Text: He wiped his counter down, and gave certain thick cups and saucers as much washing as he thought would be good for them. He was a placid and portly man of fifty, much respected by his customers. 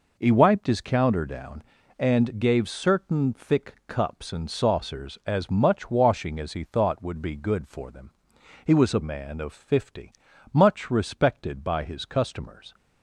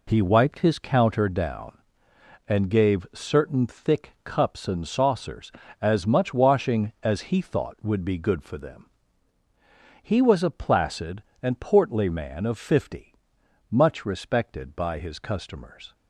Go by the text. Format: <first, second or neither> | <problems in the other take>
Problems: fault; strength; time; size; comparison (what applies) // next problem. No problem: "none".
second | skips "placid and portly"; at 9.0 s